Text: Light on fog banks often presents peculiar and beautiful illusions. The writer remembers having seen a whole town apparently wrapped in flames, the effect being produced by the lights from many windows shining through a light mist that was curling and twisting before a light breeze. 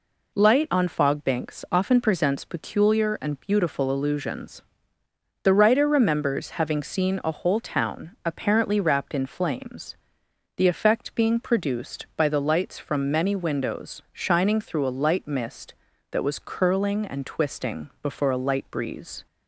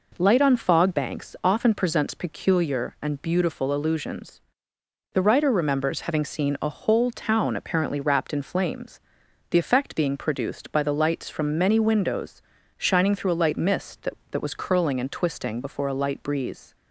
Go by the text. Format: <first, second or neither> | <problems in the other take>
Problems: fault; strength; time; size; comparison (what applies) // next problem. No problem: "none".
first | pauses between "windows" and "shining"; slight; at 12.4 s; 0.34 s long // says "that" twice; at 14.2 s